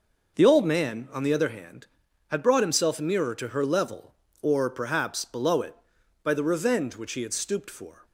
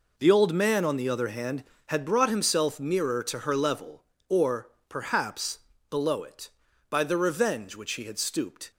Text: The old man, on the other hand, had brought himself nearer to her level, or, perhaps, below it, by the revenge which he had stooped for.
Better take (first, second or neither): first